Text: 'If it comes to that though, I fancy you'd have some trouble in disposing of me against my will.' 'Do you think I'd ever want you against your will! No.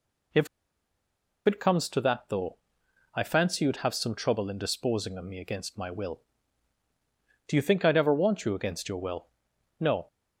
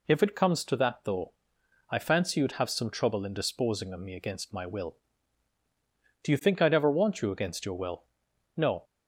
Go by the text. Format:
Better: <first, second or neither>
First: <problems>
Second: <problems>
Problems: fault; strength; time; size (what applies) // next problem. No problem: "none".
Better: second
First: pauses between "If" and "it"; at 0.4 s; 0.99 s long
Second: none